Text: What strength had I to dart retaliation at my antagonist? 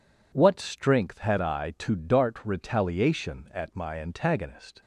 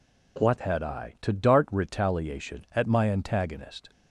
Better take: first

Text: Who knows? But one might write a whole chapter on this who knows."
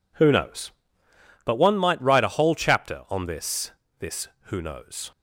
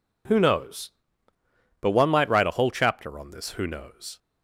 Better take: second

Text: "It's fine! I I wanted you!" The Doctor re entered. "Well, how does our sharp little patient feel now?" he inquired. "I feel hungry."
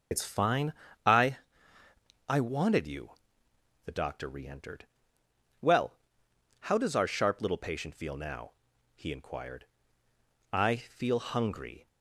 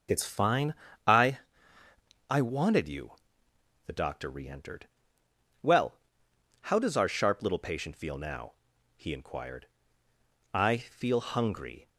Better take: second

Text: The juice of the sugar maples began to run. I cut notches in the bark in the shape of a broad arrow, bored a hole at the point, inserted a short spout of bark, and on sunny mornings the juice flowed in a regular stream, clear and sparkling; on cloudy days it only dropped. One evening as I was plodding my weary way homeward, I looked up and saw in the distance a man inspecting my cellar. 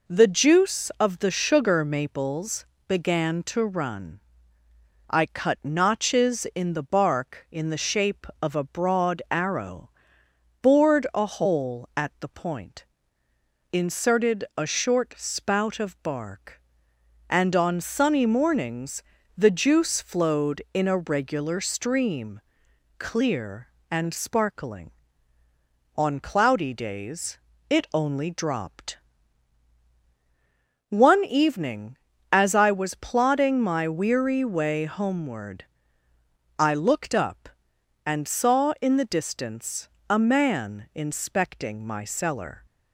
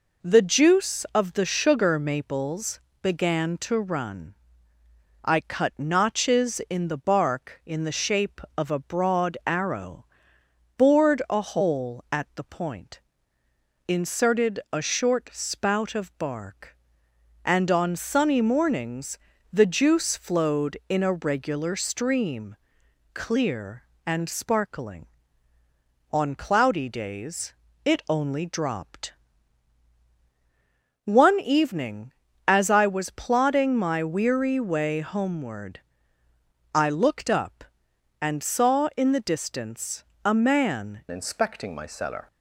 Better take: first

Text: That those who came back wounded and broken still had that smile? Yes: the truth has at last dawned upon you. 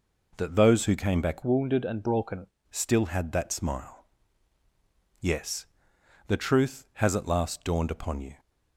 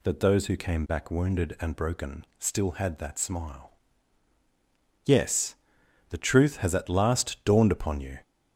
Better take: second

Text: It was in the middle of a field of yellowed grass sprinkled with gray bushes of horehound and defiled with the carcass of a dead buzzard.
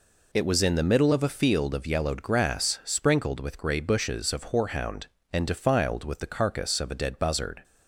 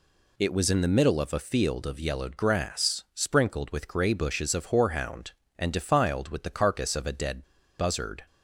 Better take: first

